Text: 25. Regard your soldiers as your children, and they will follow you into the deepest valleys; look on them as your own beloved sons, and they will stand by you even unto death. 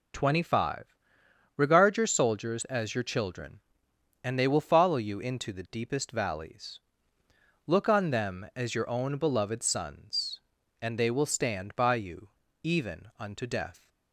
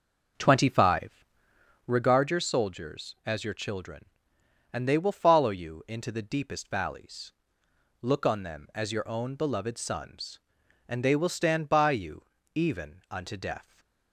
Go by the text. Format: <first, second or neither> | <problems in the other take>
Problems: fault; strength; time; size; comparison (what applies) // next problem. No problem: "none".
first | starts louder than the rest; until 1.9 s; 6 dB // pauses between "you" and "even"; slight; at 12.2 s; 0.28 s long; slight in the first // stays silent after the last word; slight; from 13.6 s on; 0.5 s long